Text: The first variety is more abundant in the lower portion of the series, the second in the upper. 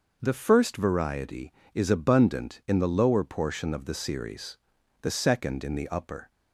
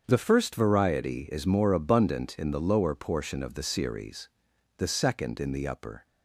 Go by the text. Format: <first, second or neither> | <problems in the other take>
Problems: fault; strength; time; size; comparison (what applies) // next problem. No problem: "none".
second | starts louder than the rest; noticeable; until 1.2 s; 6 dB; also in the second // skips "more"; at 1.8 s